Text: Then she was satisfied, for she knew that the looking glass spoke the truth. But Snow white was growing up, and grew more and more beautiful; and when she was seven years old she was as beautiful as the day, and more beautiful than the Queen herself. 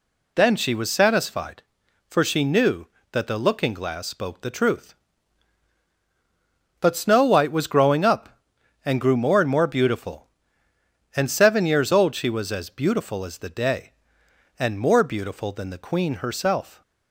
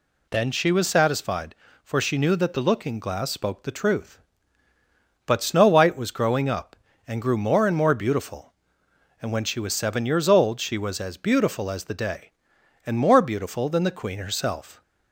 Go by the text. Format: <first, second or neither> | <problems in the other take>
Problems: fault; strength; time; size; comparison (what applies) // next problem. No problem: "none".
second | skips "when she was"; at 11.2 s